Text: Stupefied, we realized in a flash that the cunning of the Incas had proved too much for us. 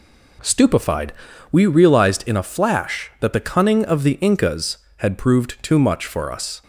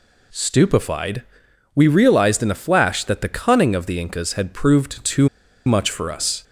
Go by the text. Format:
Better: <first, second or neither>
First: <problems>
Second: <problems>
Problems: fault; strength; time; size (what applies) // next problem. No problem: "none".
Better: first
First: none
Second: pauses between "too" and "much"; at 5.2 s; 0.38 s long